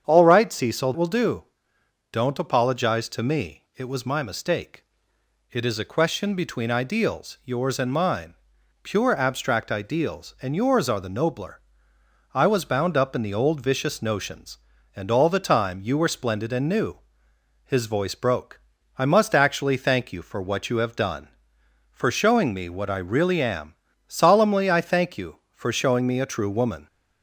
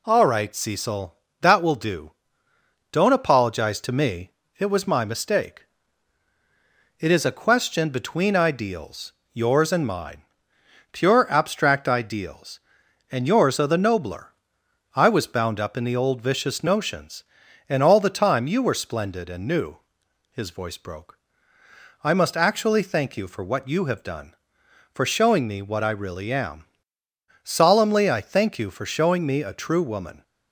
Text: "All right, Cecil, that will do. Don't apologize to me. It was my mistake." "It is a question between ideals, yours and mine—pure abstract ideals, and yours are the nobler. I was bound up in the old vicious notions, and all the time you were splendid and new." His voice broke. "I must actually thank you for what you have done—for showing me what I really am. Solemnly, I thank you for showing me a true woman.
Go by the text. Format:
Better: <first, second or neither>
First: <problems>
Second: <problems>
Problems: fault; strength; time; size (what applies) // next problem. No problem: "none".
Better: second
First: starts louder than the rest; strong; until 1.0 s; 7.5 dB // skips "that"; at 0.9 s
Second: none